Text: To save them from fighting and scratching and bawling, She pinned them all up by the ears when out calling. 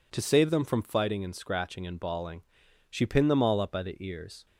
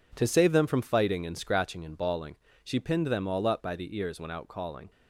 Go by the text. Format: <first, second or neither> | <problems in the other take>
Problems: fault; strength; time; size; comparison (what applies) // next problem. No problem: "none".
second | stops before "when out calling"; at 4.4 s